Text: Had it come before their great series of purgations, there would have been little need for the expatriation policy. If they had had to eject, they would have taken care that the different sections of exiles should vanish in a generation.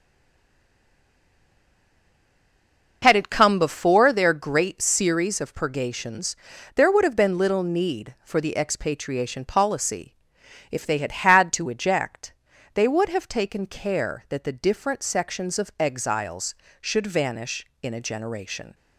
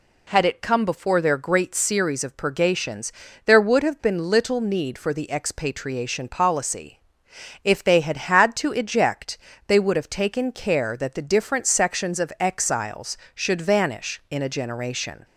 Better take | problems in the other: second | stays silent before the first word; strong; until 3.0 s; 3.0 s long

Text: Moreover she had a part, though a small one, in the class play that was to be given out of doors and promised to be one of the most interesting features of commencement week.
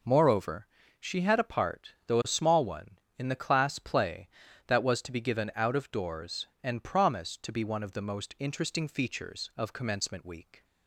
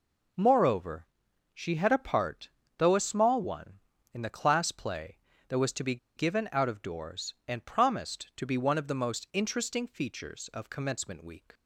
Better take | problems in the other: first | pauses between "Moreover" and "she"; noticeable; at 1.0 s; 0.48 s long; slight in the first // pauses between "be" and "given"; slight; at 5.9 s; 0.20 s long

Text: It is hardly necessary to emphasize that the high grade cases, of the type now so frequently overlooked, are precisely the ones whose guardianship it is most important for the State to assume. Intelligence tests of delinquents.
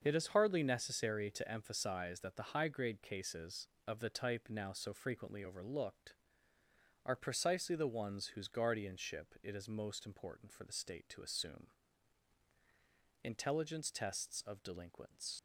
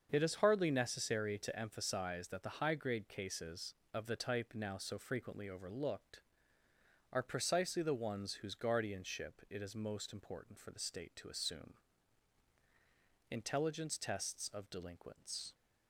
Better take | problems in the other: second | starts louder than the rest; until 1.0 s; 6.5 dB; also in the second // leaves "delinquents" unfinished; at 15.3 s; 85 ms

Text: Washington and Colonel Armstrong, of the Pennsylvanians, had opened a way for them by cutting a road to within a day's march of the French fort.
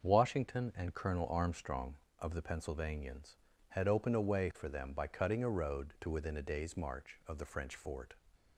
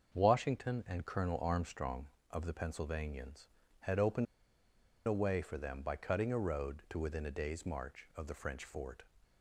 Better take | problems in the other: first | starts louder than the rest; until 1.2 s; 6.5 dB; also in the first // pauses between "opened" and "a"; noticeable; at 4.2 s; 0.81 s long

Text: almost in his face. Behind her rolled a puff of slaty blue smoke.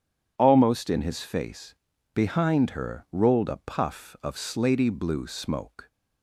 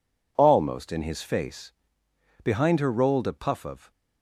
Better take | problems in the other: first | stops before "slaty blue smoke"; at 3.9 s

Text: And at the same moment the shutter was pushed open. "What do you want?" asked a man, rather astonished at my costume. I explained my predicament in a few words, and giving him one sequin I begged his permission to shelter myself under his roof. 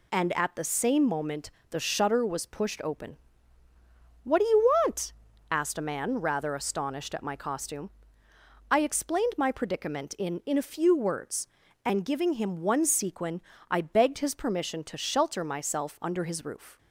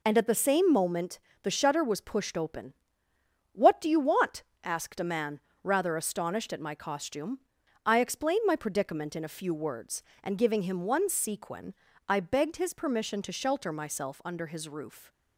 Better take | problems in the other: second | pauses between "moment" and "the"; slight; at 1.4 s; 0.20 s long; slight in the second // says "in" twice; at 10.4 s // pauses between "sequin" and "I"; slight; at 13.4 s; 0.28 s long; slight in the second

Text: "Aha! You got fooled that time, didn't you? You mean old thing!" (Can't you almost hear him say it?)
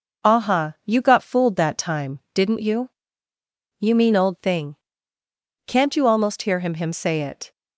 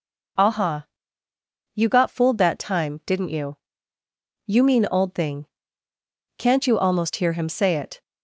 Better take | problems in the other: second | says "him" twice; at 6.7 s

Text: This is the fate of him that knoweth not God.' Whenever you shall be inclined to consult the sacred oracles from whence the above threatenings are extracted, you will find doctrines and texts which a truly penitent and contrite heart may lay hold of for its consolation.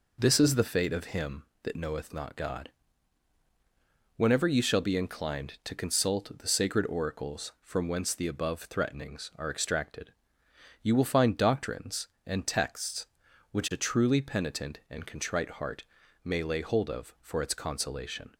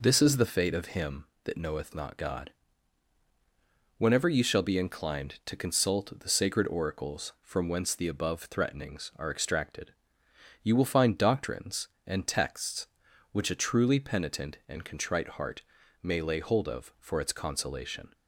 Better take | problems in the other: neither | pauses between "heart" and "may"; the same in both

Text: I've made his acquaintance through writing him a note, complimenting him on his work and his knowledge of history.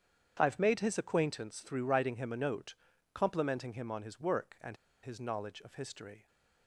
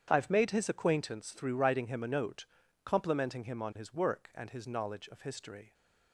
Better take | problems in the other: second | starts louder than the rest; strong; until 1.4 s; 8.5 dB; strong in the second // pauses between "and" and "his"; slight; at 4.7 s; 0.27 s long

